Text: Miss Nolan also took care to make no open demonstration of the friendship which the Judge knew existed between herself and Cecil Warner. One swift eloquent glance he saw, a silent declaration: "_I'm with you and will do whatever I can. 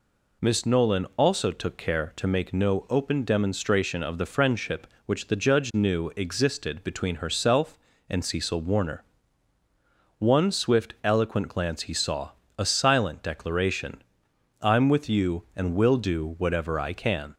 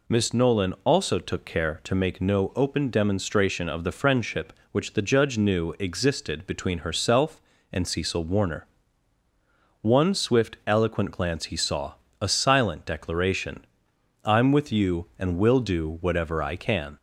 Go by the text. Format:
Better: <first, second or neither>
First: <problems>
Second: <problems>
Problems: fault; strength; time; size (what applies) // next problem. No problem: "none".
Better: neither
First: none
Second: none